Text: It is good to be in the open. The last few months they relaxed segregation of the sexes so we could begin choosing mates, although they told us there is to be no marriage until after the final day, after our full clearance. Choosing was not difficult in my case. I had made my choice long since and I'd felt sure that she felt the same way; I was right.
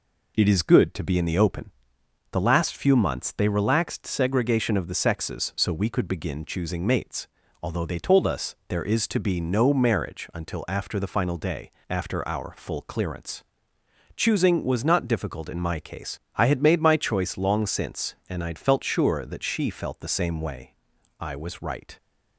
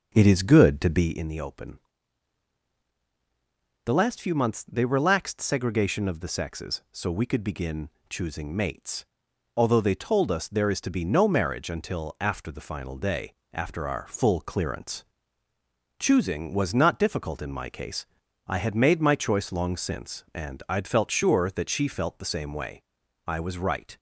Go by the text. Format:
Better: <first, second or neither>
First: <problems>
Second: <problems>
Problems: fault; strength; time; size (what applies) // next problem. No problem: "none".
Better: first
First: none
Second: starts louder than the rest; until 1.2 s; 7 dB // pauses between "begin" and "choosing"; slight; at 7.8 s; 0.22 s long